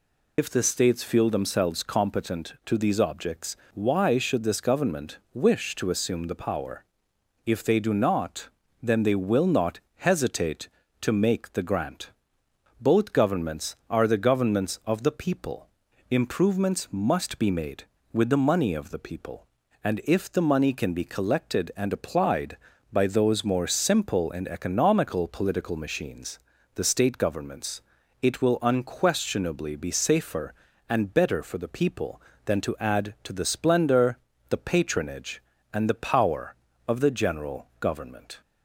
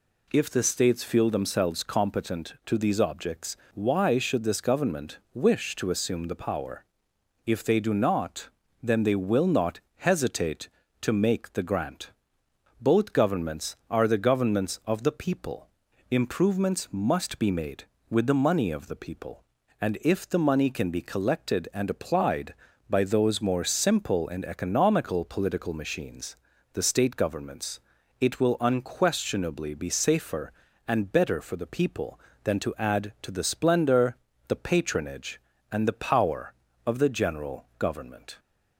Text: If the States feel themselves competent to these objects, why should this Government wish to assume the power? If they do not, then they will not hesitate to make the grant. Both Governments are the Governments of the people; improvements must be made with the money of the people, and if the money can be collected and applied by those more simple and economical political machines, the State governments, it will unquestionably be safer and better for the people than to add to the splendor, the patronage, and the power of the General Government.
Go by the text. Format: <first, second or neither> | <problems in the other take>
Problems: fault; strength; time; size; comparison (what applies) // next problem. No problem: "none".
second | loses the start of "If"; at 0.3 s; 85 ms // pauses between "not" and "hesitate"; slight; at 9.7 s; 0.18 s long; slight in the second